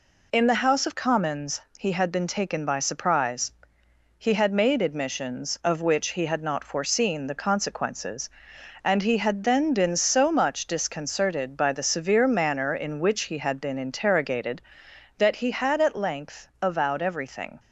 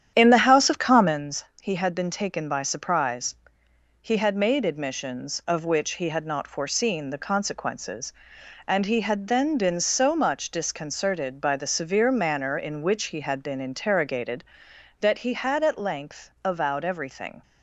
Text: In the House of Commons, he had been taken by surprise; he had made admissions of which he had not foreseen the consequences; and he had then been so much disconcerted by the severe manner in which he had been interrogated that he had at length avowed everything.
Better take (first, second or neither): first